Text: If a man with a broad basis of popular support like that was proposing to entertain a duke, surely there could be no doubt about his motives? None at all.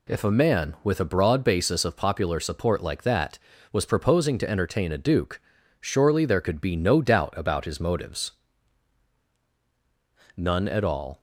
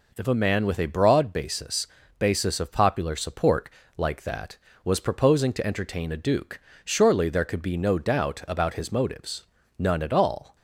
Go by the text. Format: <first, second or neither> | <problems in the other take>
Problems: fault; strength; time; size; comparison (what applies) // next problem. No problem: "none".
first | says "basis" twice; at 2.1 s // pauses between "support" and "like"; slight; at 3.6 s; 0.28 s long